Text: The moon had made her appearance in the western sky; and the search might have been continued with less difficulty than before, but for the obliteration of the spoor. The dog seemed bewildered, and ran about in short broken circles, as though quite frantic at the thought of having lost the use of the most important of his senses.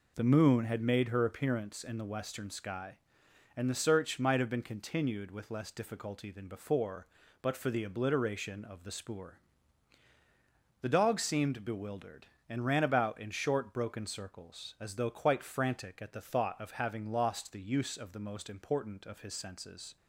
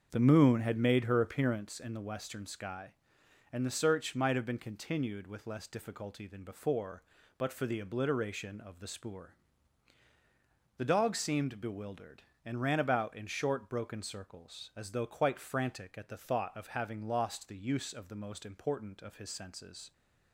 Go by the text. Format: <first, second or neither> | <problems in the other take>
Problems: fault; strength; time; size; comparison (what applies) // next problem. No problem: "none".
first | starts louder than the rest; until 1.8 s; 6.5 dB